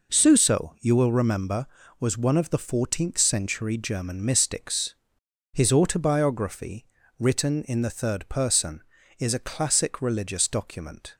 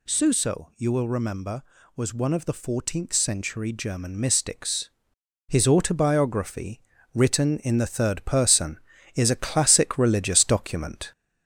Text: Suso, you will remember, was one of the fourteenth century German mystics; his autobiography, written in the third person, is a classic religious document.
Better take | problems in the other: first | gets louder; slight; throughout; 2.5 dB

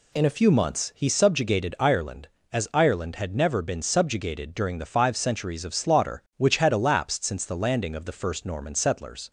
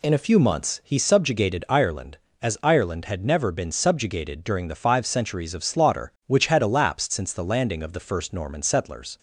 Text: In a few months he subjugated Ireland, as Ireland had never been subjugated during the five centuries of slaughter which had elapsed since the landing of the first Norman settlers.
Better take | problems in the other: neither | none

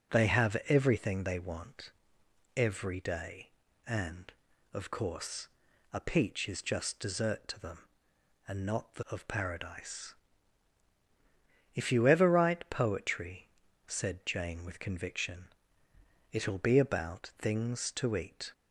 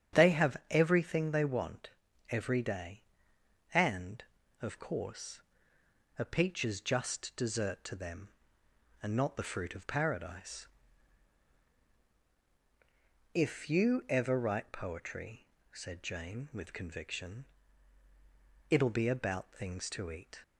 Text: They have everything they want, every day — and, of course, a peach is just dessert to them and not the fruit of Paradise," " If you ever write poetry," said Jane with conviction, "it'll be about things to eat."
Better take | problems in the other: second | starts louder than the rest; strong; until 1.2 s; 9 dB; strong in the second // skips "fruit"; at 9.0 s

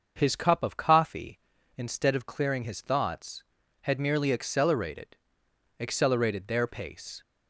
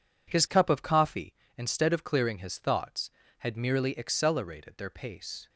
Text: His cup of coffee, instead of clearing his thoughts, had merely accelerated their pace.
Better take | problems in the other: second | starts louder than the rest; until 1.1 s; 6.5 dB // says "accelerated" twice; at 5.7 s

